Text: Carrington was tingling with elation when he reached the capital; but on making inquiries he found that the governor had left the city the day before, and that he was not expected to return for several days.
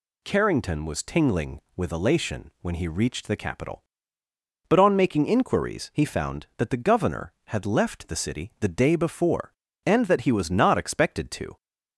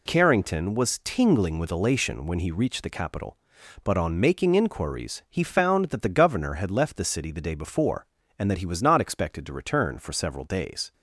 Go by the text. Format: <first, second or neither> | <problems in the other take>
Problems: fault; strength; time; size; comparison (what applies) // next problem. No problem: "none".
second | stops before "return for several days"; at 11.5 s